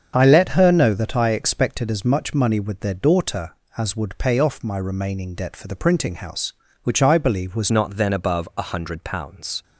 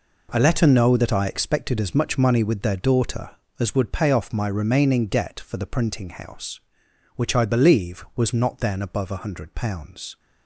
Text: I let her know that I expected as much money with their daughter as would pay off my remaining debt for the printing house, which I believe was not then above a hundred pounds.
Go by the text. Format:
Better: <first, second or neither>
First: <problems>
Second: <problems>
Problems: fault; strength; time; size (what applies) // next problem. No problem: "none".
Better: second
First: starts louder than the rest; until 1.1 s; 7 dB // changes voice at "not"; from 7.6 s on; 2.0 s long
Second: none